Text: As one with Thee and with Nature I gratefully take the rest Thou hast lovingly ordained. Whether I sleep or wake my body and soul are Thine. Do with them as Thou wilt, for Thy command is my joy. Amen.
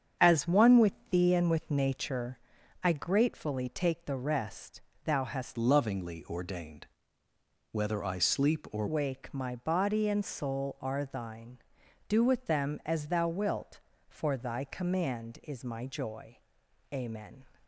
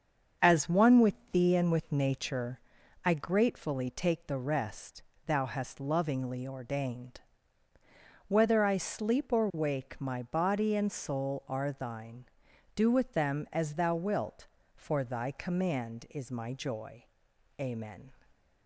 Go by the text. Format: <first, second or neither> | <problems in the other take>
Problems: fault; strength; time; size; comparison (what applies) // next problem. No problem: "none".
second | starts louder than the rest; strong; until 1.3 s; 7.5 dB; also in the second // pauses between "with" and "Thee"; slight; at 0.9 s; 0.18 s long; slight in the second // pauses between "Nature" and "I"; at 2.3 s; 0.44 s long; also in the second // pauses between "rest" and "Thou"; slight; at 4.8 s; 0.24 s long; slight in the second // changes voice from "lovingly" to "or"; from 5.5 to 8.8 s; 3.3 s long